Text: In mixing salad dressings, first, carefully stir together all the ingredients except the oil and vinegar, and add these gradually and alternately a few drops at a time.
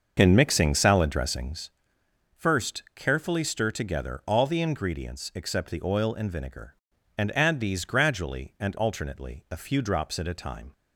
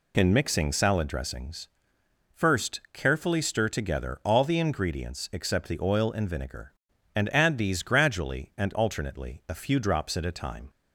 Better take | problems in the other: second | starts louder than the rest; until 1.8 s; 6.5 dB

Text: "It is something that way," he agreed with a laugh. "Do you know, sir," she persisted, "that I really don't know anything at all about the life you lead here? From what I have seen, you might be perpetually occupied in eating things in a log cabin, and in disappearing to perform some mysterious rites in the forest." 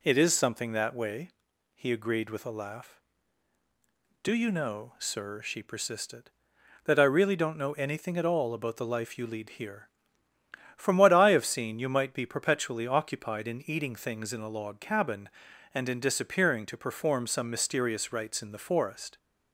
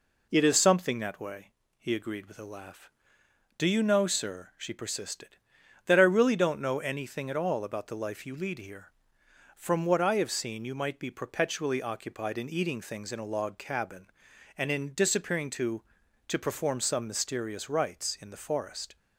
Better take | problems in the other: first | says "to" twice; at 16.2 s

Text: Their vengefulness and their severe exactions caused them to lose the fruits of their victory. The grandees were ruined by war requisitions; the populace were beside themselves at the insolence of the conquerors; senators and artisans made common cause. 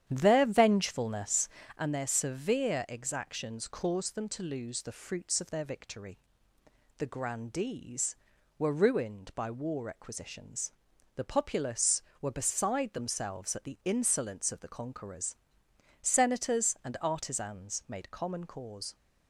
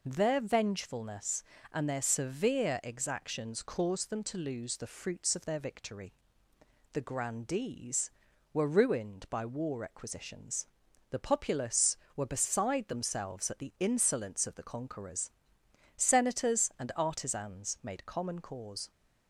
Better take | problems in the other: second | starts louder than the rest; strong; until 1.9 s; 10 dB

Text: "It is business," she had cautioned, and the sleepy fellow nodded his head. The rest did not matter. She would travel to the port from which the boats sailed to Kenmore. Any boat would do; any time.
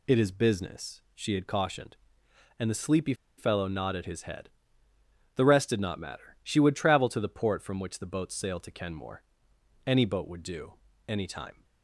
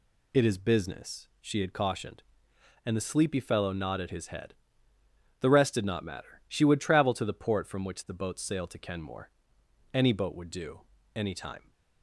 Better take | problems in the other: second | pauses between "sleepy" and "fellow"; slight; at 3.1 s; 0.24 s long

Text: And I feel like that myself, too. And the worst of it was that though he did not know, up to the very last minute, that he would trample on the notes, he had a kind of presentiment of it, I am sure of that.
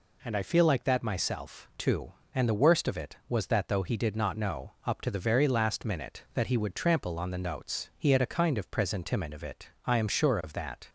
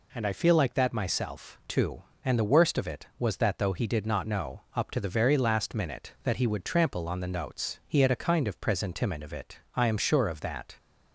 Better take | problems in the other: neither | none

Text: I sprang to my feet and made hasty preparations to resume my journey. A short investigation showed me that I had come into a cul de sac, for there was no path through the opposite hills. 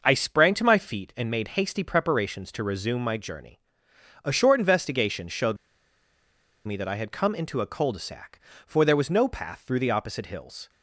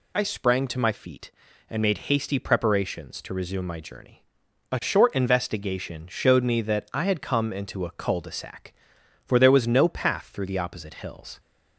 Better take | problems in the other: second | pauses between "showed" and "me"; at 5.5 s; 1.1 s long

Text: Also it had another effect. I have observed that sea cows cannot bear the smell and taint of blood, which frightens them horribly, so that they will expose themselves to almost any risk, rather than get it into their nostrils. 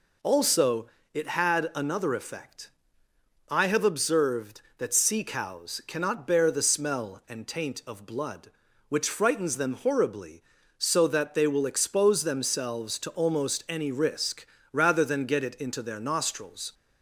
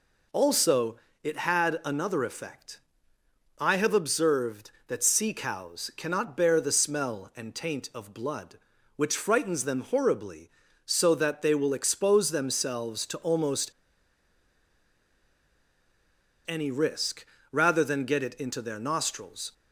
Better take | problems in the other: first | pauses between "Also" and "it"; slight; at 0.9 s; 0.26 s long; slight in the first // pauses between "almost" and "any"; strong; at 13.7 s; 2.7 s long

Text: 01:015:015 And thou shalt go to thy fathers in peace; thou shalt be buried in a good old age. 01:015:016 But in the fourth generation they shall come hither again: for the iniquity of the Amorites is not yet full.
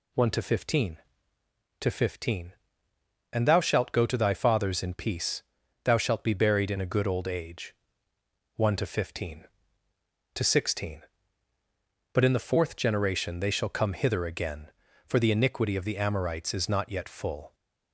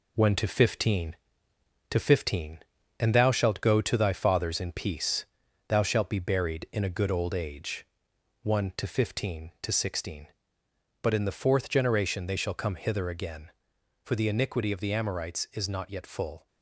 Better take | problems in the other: first | gets quieter; noticeable; throughout; 5.5 dB

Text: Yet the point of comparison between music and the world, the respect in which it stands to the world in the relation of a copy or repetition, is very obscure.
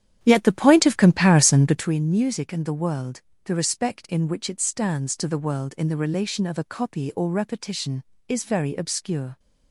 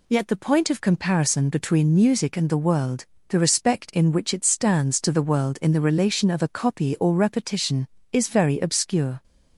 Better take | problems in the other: second | starts louder than the rest; strong; until 1.9 s; 10 dB

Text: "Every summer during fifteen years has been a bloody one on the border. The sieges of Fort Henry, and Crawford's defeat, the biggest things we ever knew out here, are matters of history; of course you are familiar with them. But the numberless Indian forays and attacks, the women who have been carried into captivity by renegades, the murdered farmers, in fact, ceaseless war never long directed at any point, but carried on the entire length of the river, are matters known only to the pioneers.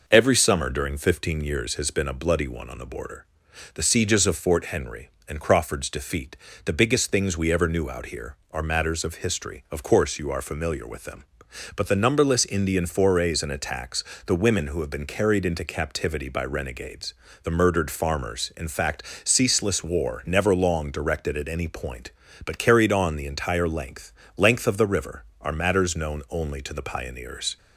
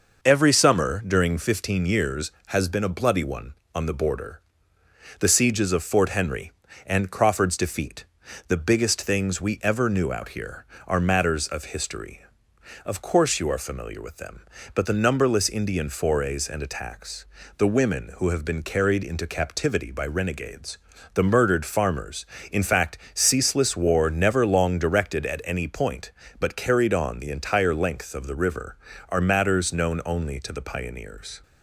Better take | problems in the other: second | says "length" twice; at 24.3 s

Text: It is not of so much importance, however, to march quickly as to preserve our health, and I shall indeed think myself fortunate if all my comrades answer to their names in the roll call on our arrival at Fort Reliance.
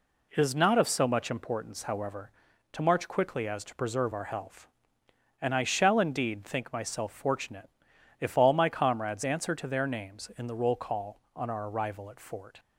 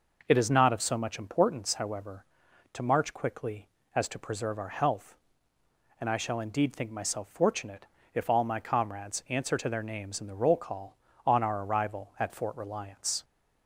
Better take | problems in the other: second | pauses between "fortunate" and "if"; noticeable; at 7.6 s; 0.50 s long; slight in the second // stops before "Reliance"; at 12.5 s

